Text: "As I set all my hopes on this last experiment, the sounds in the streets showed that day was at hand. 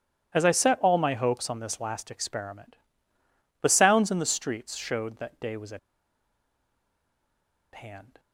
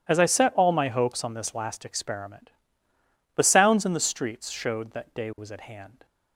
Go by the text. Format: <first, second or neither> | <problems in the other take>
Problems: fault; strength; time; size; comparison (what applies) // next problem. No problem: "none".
second | starts louder than the rest; strong; until 1.3 s; 11 dB; strong in the second // pauses between "at" and "hand"; strong; at 5.7 s; 1.9 s long